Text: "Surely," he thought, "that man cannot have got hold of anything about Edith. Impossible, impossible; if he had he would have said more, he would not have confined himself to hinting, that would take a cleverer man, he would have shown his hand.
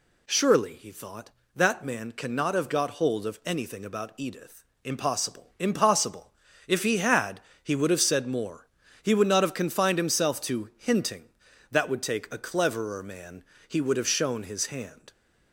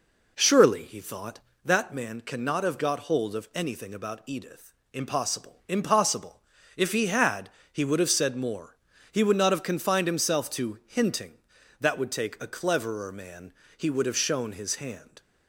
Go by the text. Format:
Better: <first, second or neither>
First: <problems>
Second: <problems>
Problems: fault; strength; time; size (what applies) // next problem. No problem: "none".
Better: first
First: pauses between "had" and "he"; slight; at 7.3 s; 0.22 s long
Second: starts louder than the rest; noticeable; until 1.7 s; 4 dB // pauses between "had" and "he"; slight; at 7.4 s; 0.22 s long